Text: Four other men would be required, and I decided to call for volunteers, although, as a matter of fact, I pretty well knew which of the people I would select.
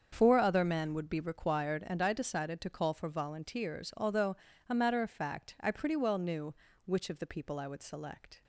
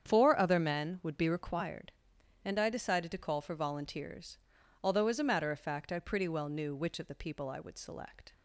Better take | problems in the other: second | starts louder than the rest; until 1.1 s; 7 dB; strong in the second // skips "as"; at 4.5 s

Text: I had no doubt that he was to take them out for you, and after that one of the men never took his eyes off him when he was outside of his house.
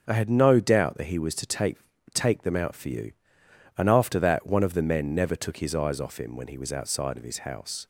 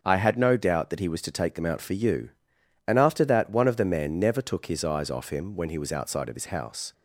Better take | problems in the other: second | starts louder than the rest; until 1.0 s; 7 dB; also in the second // says "take" twice; at 2.1 s

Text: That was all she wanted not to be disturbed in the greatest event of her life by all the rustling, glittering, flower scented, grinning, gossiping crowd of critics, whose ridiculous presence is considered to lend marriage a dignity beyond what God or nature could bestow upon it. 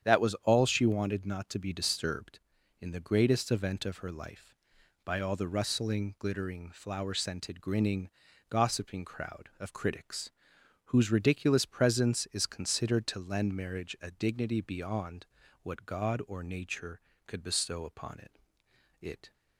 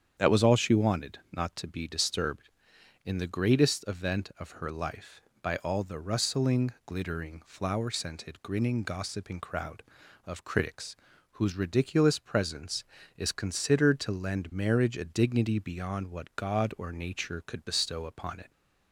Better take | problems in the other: second | starts louder than the rest; strong; until 1.1 s; 9 dB; strong in the second // pauses between "beyond" and "what"; slight; at 15.2 s; 0.36 s long // says "it" twice; at 19.0 s

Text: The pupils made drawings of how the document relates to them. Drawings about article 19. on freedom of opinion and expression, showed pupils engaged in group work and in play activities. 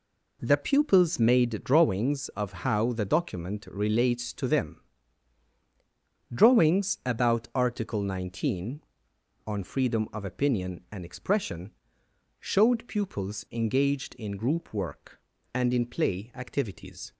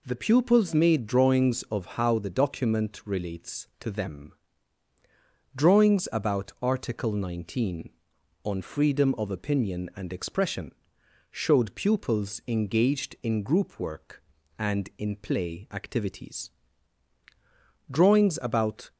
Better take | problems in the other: first | goes on to say "Drawings about"; noticeable; from 17.8 s on; 1.0 s long

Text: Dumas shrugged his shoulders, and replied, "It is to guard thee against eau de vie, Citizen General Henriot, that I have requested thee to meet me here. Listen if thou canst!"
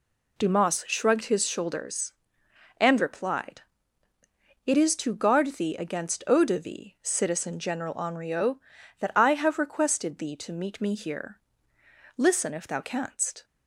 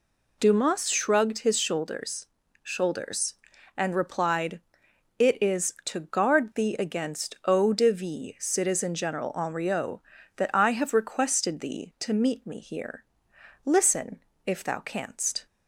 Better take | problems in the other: first | says "shoulders" twice; at 2.6 s // pauses between "Listen" and "if"; slight; at 14.1 s; 0.26 s long

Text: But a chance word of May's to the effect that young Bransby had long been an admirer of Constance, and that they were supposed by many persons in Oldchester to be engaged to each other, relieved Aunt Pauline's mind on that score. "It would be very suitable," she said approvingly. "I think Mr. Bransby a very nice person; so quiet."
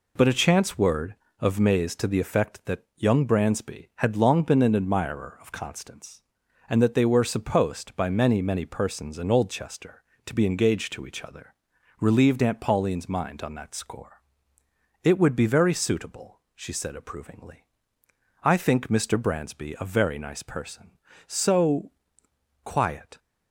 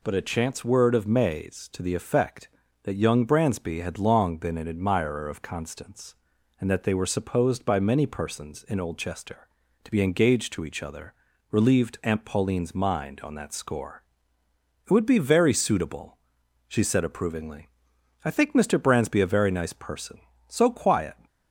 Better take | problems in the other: second | says "many" twice; at 8.4 s // pauses between "so" and "quiet"; noticeable; at 21.9 s; 0.74 s long

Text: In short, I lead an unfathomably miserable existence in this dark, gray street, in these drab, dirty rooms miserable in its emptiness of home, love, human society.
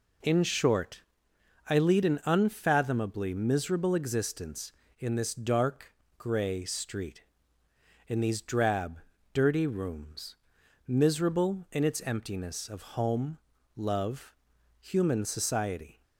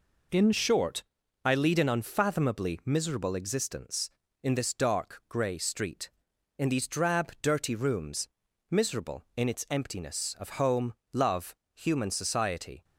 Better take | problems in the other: first | changes voice at "short"; from 0.5 s on; 12.3 s long // pauses between "rooms" and "miserable"; at 8.2 s; 0.42 s long; noticeable in the first

